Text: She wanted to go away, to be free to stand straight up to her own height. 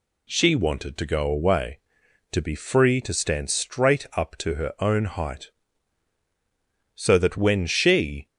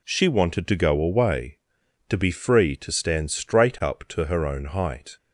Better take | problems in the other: second | goes on to say "So that when she"; noticeable; from 6.9 s on; 1.2 s long

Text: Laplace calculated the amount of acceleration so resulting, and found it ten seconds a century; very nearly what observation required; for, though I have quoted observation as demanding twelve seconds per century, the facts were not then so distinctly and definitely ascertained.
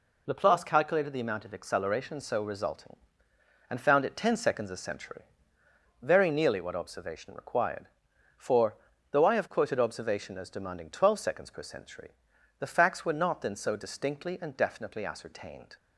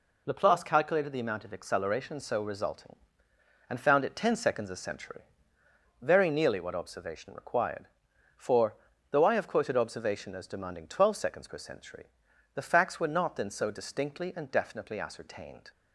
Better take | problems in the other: neither | none

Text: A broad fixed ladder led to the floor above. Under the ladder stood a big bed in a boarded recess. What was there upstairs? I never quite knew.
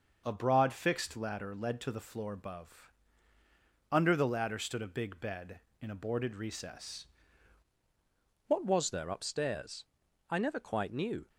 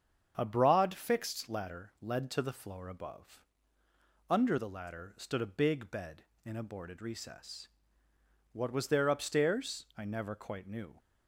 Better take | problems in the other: second | starts louder than the rest; until 1.2 s; 6 dB; strong in the second // changes voice at "What"; from 8.4 s on; 2.8 s long

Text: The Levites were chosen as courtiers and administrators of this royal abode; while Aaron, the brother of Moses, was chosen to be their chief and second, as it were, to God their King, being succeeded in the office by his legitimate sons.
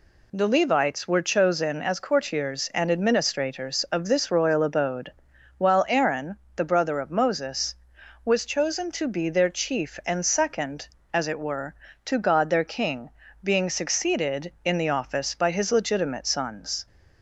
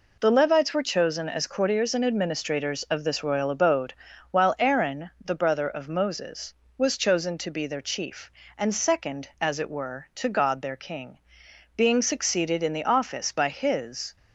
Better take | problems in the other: first | stops before "legitimate sons"; at 14.1 s

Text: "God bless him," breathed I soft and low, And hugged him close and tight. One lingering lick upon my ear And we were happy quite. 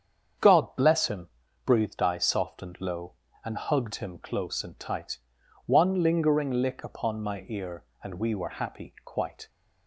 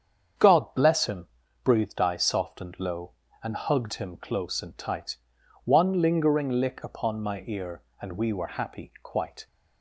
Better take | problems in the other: neither | starts louder than the rest; strong; the same in both

